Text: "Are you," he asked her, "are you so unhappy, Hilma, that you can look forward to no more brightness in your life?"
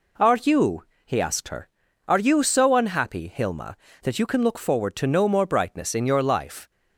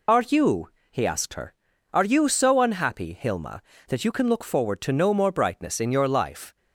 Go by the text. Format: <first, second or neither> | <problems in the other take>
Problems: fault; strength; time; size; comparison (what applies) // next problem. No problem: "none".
first | loses the start of "Are"; at 0.0 s; 65 ms